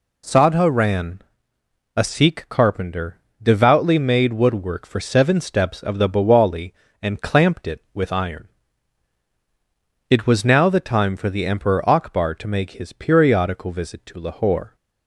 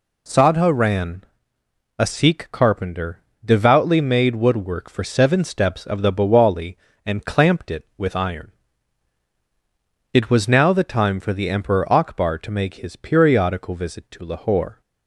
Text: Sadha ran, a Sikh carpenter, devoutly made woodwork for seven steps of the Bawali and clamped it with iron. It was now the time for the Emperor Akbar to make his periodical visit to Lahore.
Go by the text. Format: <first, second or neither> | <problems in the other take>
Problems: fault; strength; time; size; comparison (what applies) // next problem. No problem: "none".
neither | none